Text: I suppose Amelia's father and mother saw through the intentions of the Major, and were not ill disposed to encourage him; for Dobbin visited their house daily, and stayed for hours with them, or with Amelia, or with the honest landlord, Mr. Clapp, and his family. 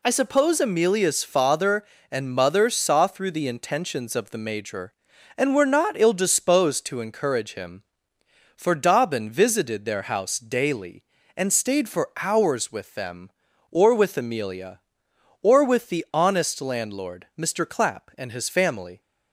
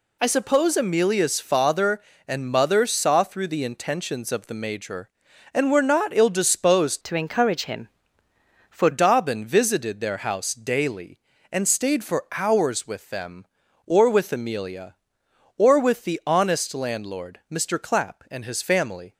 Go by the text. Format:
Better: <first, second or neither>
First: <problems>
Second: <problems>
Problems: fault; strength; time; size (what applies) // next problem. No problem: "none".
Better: first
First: none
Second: changes voice from "to" to "for"; from 7.0 to 8.8 s; 1.8 s long